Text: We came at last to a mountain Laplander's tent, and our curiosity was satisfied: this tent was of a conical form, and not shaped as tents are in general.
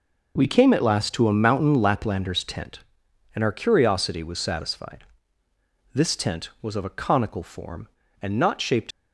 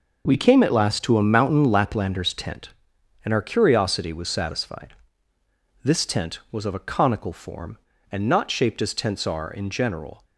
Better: second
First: stops before "as tents are in general"; at 8.9 s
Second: none

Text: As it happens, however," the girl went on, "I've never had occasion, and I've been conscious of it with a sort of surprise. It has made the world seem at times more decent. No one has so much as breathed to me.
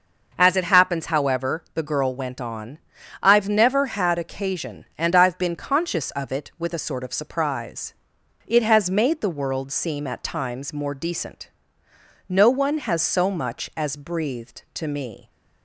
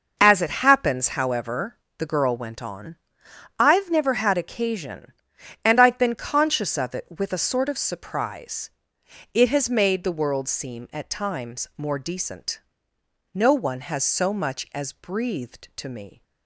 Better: neither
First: none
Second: none

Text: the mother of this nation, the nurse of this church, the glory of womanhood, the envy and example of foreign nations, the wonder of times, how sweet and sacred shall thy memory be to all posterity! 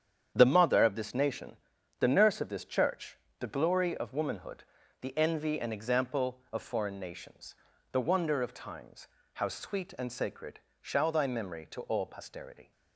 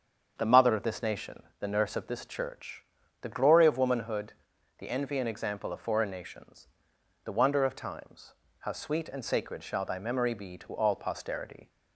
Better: second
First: starts louder than the rest; strong; until 1.3 s; 8.5 dB // pauses between "sacred" and "shall"; slight; at 10.5 s; 0.22 s long // skips "be"; at 11.6 s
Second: starts louder than the rest; strong; until 1.3 s; 7.5 dB

